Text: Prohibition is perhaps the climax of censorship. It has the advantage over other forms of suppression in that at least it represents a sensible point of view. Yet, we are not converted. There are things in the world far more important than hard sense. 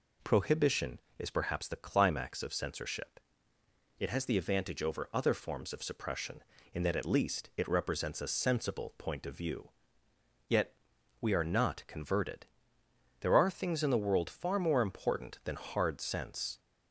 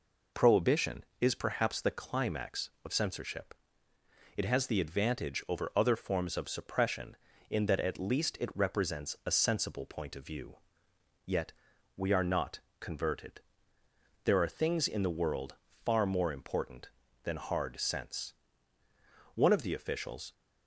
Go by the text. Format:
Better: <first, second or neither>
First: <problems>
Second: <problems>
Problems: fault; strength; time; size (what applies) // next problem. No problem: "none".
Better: first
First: none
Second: pauses between "not" and "converted"; slight; at 12.6 s; 0.18 s long // pauses between "world" and "far"; slight; at 15.5 s; 0.30 s long // goes on to say "One of the officials"; noticeable; from 19.3 s on; 0.98 s long